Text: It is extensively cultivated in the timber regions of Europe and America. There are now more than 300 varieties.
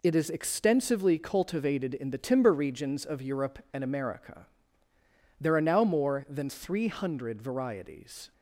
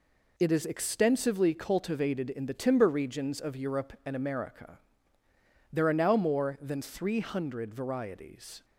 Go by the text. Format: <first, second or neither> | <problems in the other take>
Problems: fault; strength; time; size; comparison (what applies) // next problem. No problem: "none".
neither | none